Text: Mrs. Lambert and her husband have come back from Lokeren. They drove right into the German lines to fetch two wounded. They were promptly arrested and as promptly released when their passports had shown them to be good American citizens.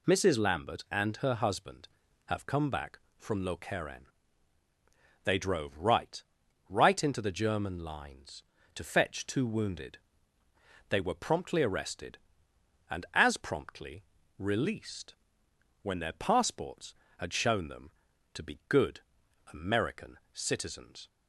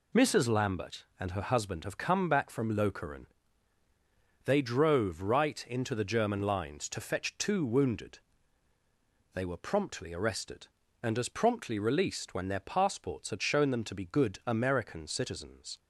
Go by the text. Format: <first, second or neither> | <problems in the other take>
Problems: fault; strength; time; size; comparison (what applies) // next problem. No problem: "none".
second | says "right" twice; at 6.6 s // pauses between "promptly" and "released"; slight; at 14.0 s; 0.34 s long // pauses between "released" and "when"; noticeable; at 15.1 s; 0.66 s long // pauses between "good" and "American"; noticeable; at 18.9 s; 0.52 s long